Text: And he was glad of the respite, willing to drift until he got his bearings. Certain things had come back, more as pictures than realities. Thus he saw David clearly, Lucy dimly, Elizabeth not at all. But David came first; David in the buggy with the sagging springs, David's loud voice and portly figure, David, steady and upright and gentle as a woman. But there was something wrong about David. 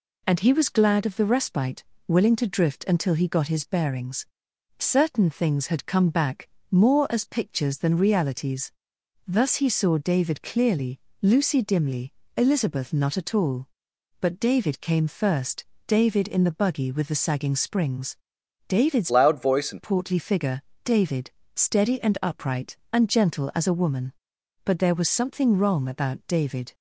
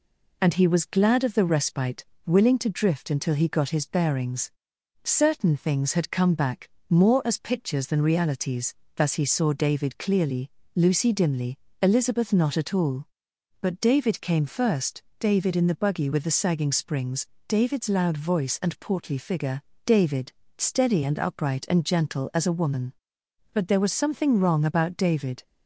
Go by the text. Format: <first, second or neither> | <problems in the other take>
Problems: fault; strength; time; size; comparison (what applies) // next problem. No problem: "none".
second | changes voice from "loud" to "and"; from 19.1 to 19.8 s; 0.7 s long